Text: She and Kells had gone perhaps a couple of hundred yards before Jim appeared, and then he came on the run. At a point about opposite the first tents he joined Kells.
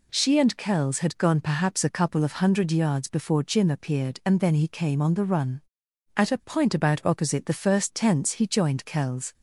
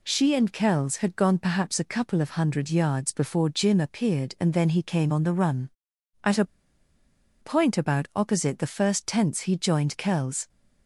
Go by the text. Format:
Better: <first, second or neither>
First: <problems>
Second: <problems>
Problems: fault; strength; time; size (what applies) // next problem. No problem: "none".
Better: first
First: none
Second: pauses between "a" and "point"; noticeable; at 6.4 s; 0.97 s long